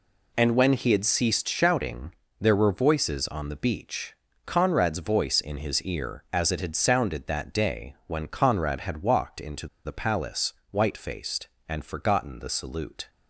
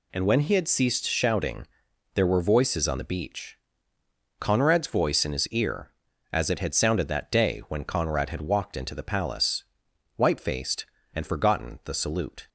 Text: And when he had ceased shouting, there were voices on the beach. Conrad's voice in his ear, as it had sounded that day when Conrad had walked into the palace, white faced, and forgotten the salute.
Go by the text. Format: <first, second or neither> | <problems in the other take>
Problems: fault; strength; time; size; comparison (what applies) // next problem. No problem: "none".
second | pauses between "into" and "the"; slight; at 9.6 s; 0.18 s long